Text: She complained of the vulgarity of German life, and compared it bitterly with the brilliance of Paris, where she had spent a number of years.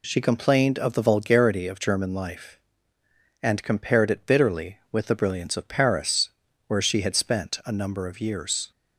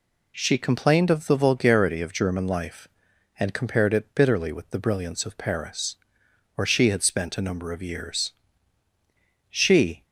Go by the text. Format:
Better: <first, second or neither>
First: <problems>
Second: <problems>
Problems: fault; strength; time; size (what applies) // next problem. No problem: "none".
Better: first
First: none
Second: goes on to say "She"; from 9.4 s on; 0.56 s long